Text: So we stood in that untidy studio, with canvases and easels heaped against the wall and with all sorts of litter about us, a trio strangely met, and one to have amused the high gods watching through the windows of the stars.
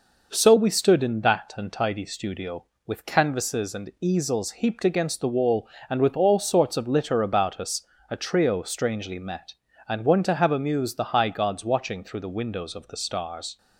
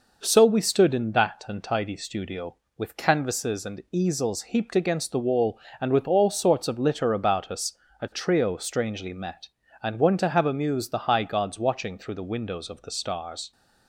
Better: neither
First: none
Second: none

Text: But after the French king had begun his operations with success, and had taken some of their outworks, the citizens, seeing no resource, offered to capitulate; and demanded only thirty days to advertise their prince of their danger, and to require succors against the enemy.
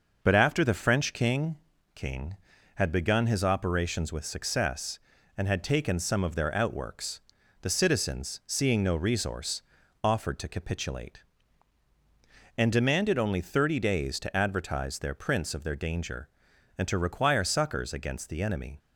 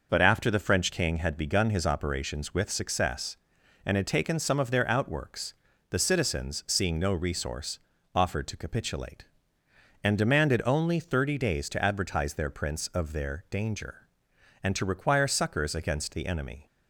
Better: second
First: says "king" twice; at 1.9 s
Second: none

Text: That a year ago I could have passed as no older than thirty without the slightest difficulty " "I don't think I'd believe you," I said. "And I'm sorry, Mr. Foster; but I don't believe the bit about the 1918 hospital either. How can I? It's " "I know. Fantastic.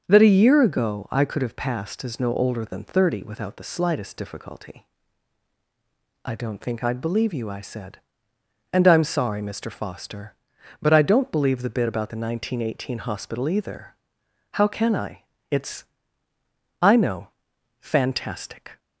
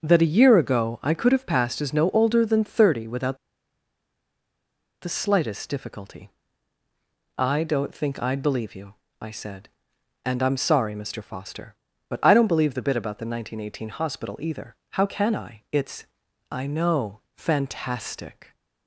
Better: first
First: starts louder than the rest; until 1.0 s; 7 dB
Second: starts louder than the rest; until 1.0 s; 7 dB // pauses between "without" and "the"; strong; at 3.3 s; 1.6 s long

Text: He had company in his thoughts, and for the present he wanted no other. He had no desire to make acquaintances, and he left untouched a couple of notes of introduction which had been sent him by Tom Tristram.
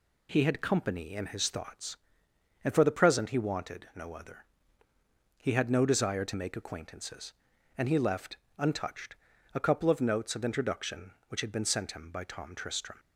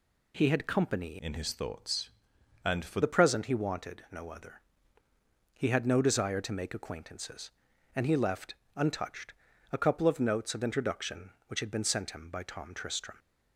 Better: first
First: pauses between "left" and "untouched"; slight; at 8.3 s; 0.22 s long // pauses between "untouched" and "a"; at 9.1 s; 0.40 s long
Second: changes voice from "in" to "for"; from 1.1 to 3.0 s; 1.9 s long // pauses between "left" and "untouched"; slight; at 8.5 s; 0.22 s long // pauses between "untouched" and "a"; at 9.3 s; 0.40 s long

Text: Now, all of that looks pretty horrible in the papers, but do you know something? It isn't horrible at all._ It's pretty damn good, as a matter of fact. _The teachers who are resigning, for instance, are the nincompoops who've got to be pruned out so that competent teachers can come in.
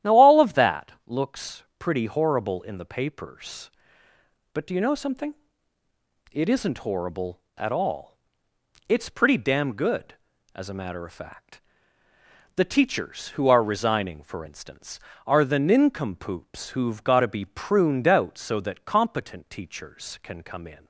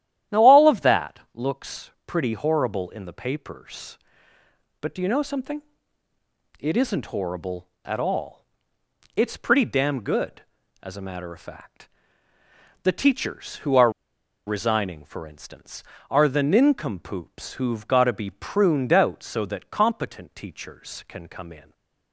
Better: first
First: starts louder than the rest; strong; until 1.1 s; 11.5 dB // pauses between "looks" and "pretty"; slight; at 1.6 s; 0.16 s long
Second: starts louder than the rest; strong; until 1.4 s; 11.5 dB // pauses between "looks" and "pretty"; slight; at 1.9 s; 0.16 s long // pauses between "are" and "resigning"; noticeable; at 13.9 s; 0.56 s long // stays silent after the last word; slight; from 21.6 s on; 0.5 s long

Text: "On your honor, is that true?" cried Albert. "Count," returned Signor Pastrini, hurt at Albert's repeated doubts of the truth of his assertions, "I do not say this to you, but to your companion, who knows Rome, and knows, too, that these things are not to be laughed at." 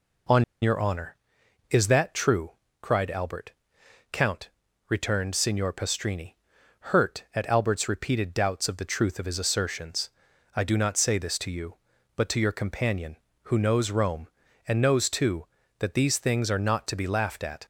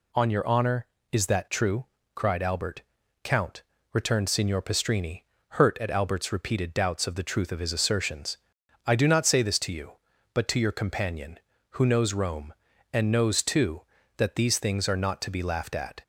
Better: second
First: pauses between "On" and "your"; slight; at 0.4 s; 0.18 s long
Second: none

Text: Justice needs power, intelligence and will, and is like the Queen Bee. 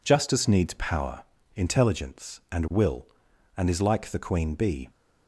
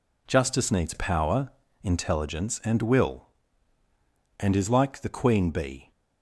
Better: neither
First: none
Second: none

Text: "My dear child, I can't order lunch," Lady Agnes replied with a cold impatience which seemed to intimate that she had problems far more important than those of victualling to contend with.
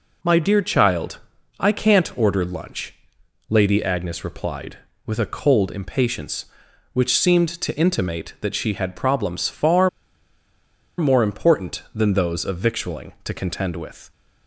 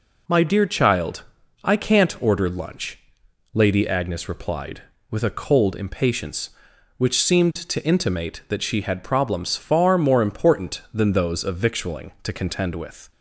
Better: second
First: pauses between "far" and "more"; at 9.8 s; 1.1 s long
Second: none

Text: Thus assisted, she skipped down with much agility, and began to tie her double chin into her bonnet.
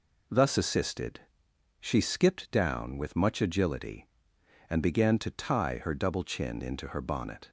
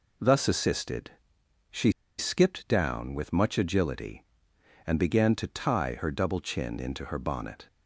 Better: first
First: none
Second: pauses between "she" and "skipped"; slight; at 1.9 s; 0.26 s long

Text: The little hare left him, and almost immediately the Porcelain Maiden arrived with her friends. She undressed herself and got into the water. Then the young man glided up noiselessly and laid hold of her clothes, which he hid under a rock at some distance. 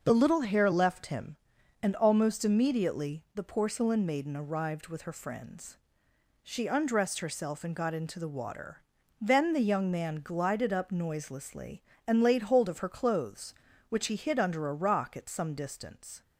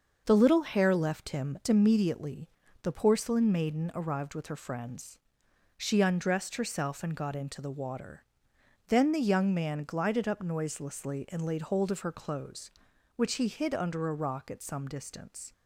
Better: first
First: starts louder than the rest; until 1.0 s; 6.5 dB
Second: starts louder than the rest; until 1.2 s; 6.5 dB // skips "and almost"; at 1.6 s // pauses between "immediately" and "the"; slight; at 2.4 s; 0.36 s long

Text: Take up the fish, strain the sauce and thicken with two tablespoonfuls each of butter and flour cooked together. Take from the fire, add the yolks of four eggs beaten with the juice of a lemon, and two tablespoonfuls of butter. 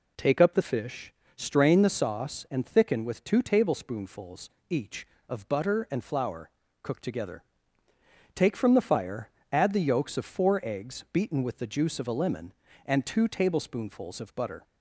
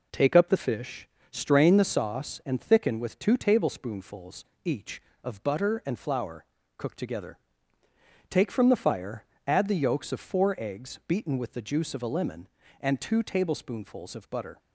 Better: first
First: pauses between "tablespoonfuls" and "each"; slight; at 4.4 s; 0.20 s long // pauses between "flour" and "cooked"; slight; at 6.4 s; 0.32 s long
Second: gets quieter; throughout; 4 dB // pauses between "tablespoonfuls" and "each"; slight; at 4.4 s; 0.20 s long // pauses between "flour" and "cooked"; slight; at 6.4 s; 0.32 s long

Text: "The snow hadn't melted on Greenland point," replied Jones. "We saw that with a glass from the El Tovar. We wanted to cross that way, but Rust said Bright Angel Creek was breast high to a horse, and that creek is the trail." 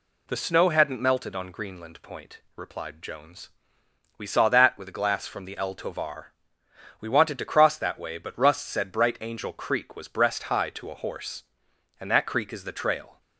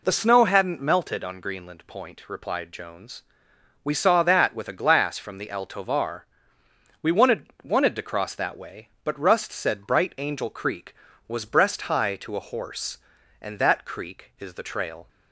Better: first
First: none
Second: says "wanted" twice; at 7.6 s

